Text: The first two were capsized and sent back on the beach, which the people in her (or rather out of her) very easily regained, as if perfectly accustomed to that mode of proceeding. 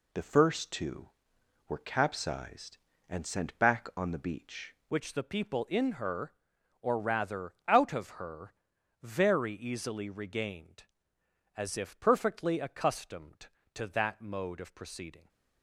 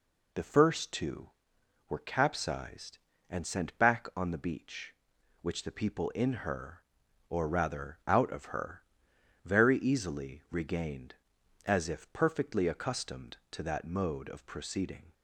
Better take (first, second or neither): second